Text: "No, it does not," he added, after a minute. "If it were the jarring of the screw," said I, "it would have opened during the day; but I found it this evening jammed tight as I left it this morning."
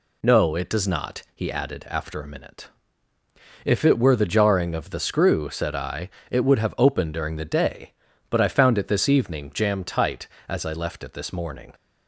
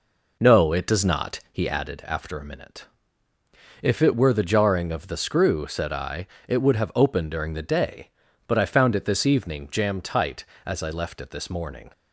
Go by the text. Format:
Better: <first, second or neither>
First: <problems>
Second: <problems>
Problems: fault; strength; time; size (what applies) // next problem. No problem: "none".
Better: first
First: none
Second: starts louder than the rest; noticeable; until 1.9 s; 4 dB